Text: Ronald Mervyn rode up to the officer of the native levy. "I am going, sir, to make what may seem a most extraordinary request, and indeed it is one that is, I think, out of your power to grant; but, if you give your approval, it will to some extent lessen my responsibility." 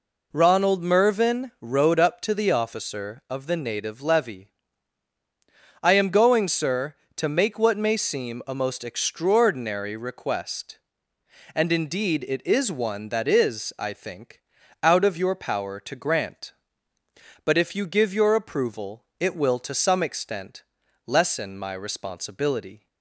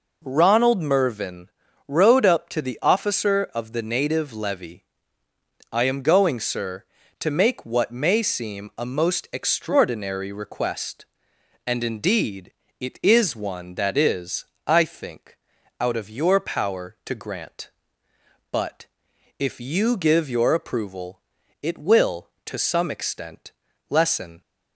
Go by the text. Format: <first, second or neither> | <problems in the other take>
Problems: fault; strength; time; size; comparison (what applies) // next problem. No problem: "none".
first | pauses between "Mervyn" and "rode"; at 1.4 s; 0.40 s long // pauses between "indeed" and "it"; slight; at 12.5 s; 0.26 s long // pauses between "extent" and "lessen"; at 23.5 s; 0.38 s long; also in the first // stops before "my responsibility"; at 24.4 s